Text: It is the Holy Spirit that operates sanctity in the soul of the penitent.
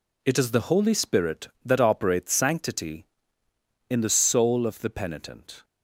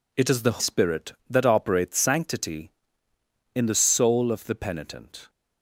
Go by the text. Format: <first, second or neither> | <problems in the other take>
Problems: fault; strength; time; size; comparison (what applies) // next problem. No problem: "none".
first | skips "Holy"; at 0.5 s